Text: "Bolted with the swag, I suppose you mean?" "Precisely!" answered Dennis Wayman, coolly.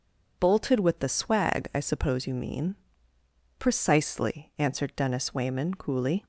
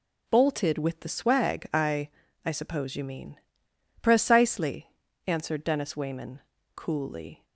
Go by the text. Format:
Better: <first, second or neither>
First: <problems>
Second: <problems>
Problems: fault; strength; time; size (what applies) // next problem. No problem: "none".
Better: first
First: none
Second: says "I" twice; at 2.4 s